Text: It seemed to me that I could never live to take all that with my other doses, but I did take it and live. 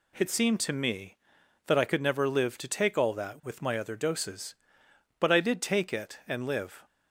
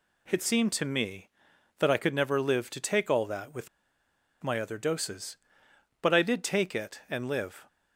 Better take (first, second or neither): first